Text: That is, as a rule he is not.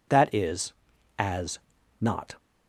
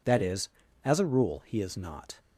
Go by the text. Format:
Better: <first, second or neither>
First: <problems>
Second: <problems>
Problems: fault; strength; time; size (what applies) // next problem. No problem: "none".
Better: second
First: skips "a rule he is"; at 1.7 s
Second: none